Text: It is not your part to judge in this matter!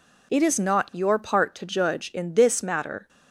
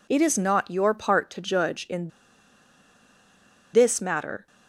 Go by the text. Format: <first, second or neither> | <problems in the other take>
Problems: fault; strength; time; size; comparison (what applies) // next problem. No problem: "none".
first | pauses between "in" and "this"; strong; at 2.0 s; 1.6 s long